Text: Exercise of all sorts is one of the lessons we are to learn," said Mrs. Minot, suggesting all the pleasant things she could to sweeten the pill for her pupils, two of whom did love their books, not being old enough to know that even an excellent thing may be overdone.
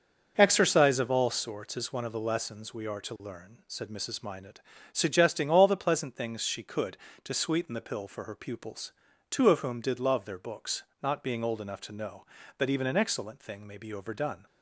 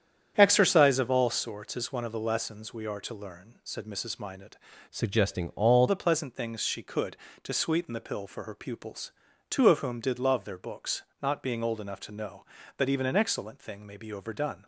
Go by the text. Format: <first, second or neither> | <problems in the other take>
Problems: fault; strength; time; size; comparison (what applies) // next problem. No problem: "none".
first | starts louder than the rest; strong; until 1.3 s; 9 dB // changes voice from "suggesting" to "all"; from 4.9 to 5.8 s; 0.9 s long